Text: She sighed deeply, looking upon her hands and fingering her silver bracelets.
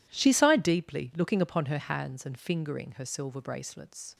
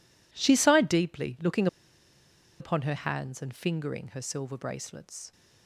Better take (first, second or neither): first